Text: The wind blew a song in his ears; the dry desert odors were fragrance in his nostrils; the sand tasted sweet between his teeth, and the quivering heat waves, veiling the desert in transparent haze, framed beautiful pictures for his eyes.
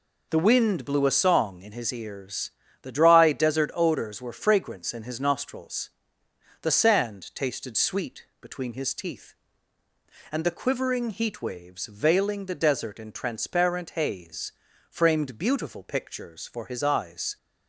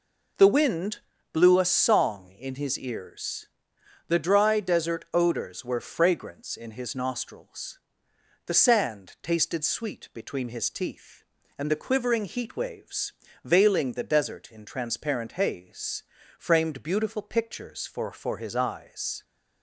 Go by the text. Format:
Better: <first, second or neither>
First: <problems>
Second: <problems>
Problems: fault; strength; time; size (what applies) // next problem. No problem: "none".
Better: first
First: none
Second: pauses between "wind" and "blew"; slight; at 0.9 s; 0.32 s long // says "for" twice; at 18.1 s